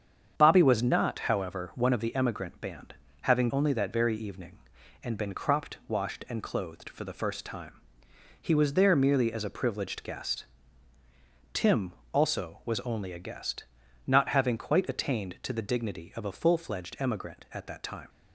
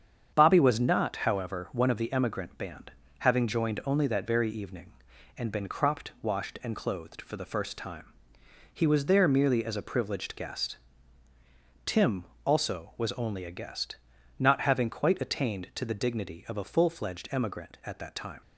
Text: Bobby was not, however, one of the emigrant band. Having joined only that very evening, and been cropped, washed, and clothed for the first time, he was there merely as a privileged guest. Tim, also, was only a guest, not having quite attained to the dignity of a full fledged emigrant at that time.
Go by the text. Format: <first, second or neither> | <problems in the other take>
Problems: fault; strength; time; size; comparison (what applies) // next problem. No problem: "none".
second | starts louder than the rest; strong; until 1.3 s; 8 dB; strong in the second // skips "joined"; at 3.5 s